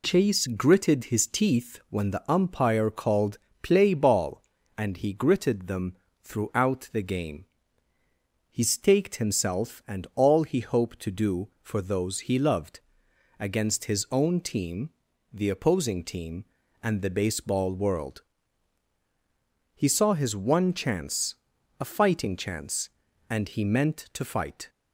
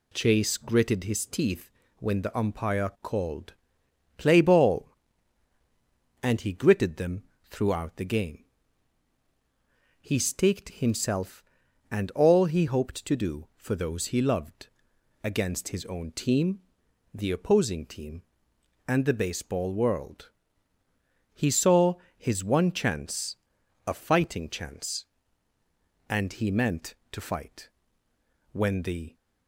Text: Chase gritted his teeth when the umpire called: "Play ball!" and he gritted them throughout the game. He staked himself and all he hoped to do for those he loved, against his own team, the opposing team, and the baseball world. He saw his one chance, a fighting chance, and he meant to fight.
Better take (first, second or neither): first